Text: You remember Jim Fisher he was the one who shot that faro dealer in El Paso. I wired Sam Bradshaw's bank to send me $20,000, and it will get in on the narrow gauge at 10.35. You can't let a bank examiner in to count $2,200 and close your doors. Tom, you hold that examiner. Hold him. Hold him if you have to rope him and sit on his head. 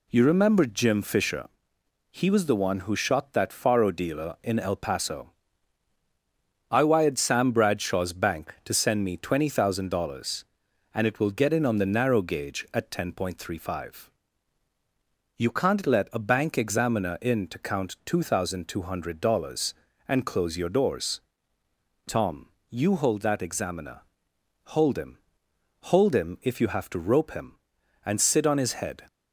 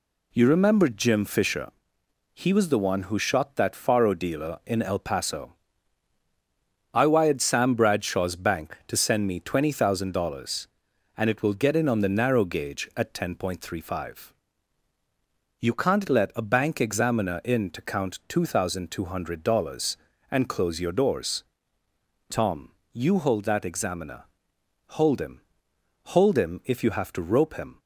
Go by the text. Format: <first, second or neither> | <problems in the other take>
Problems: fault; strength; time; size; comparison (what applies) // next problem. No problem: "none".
first | pauses between "Fisher" and "he"; noticeable; at 1.7 s; 0.64 s long; noticeable in the first // stops before "and sit on his head"; at 27.7 s